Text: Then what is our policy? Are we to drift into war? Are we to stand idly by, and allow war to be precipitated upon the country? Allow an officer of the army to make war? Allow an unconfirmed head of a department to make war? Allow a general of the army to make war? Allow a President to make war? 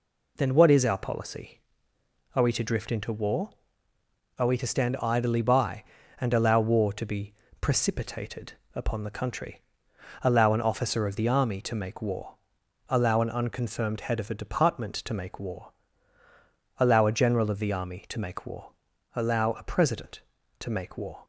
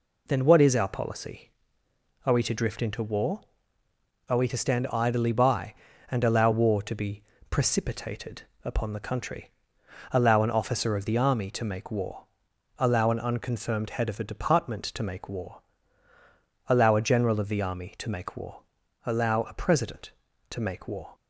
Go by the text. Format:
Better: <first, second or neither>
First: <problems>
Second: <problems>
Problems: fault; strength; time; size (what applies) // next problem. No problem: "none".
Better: neither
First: pauses between "be" and "precipitated"; slight; at 7.3 s; 0.28 s long // pauses between "precipitated" and "upon"; slight; at 8.5 s; 0.20 s long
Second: pauses between "be" and "precipitated"; slight; at 7.2 s; 0.28 s long // pauses between "precipitated" and "upon"; slight; at 8.4 s; 0.20 s long